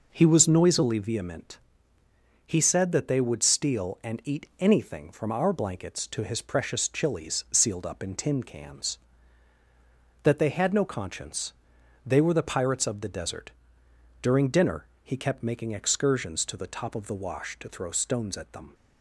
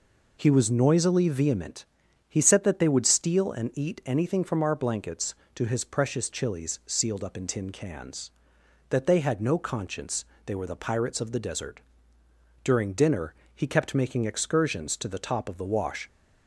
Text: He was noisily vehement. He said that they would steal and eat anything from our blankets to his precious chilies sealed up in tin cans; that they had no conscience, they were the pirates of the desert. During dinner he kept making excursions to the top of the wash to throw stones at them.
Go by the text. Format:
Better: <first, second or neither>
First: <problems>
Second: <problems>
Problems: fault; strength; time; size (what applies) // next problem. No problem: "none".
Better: first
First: pauses between "dinner" and "he"; slight; at 14.8 s; 0.18 s long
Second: pauses between "dinner" and "he"; slight; at 13.3 s; 0.22 s long // stops before "to throw stones at them"; at 16.0 s